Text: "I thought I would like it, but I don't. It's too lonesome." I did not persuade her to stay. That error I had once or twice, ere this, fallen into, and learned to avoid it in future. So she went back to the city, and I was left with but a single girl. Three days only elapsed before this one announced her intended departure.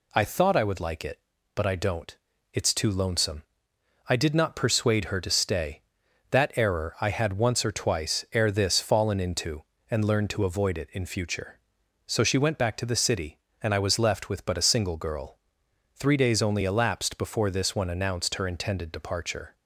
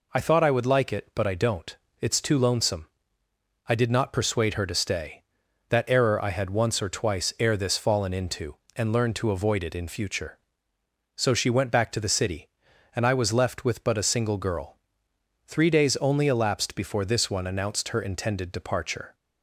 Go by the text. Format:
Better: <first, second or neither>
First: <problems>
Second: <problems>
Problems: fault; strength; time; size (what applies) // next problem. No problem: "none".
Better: neither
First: none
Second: none